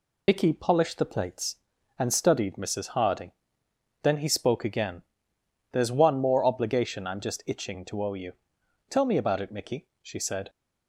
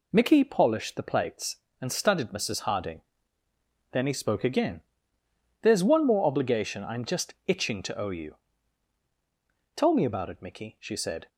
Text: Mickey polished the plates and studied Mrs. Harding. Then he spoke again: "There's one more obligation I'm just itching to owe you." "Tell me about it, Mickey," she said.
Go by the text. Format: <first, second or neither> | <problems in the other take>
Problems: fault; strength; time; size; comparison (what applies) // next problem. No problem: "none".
second | loses the start of "Mickey"; at 0.2 s; 75 ms